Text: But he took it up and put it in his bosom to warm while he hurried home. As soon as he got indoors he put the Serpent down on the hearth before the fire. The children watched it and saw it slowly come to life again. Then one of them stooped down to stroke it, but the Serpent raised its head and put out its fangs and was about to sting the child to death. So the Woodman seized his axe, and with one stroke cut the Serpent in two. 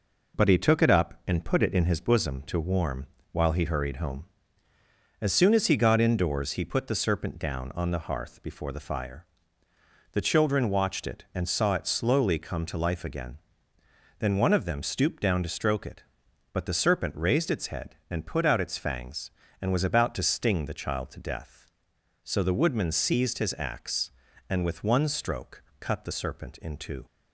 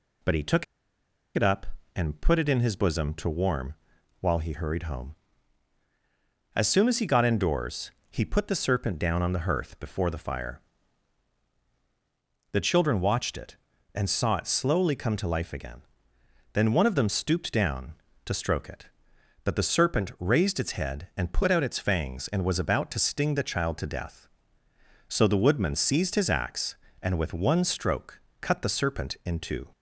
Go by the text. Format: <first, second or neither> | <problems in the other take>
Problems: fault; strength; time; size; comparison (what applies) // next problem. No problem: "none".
first | pauses between "took" and "it"; noticeable; at 0.6 s; 0.70 s long // pauses between "warm" and "while"; noticeable; at 3.7 s; 0.46 s long; slight in the first // pauses between "indoors" and "he"; slight; at 7.9 s; 0.22 s long // pauses between "stroke" and "cut"; slight; at 28.1 s; 0.22 s long; slight in the first